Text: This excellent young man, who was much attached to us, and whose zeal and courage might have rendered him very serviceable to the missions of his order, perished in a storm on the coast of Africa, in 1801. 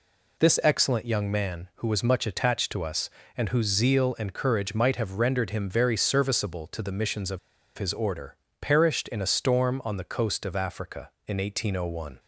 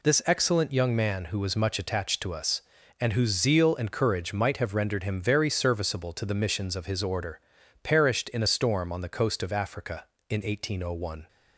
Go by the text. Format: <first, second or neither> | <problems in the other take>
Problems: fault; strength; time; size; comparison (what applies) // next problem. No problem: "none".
second | pauses between "of" and "his"; at 7.3 s; 0.38 s long